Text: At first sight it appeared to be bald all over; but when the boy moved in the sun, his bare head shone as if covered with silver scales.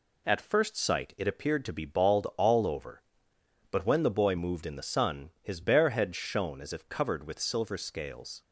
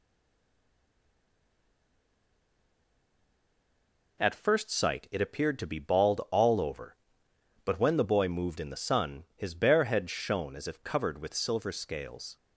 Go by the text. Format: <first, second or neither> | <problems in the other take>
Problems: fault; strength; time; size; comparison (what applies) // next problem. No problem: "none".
first | stays silent before the first word; strong; until 4.1 s; 4.1 s long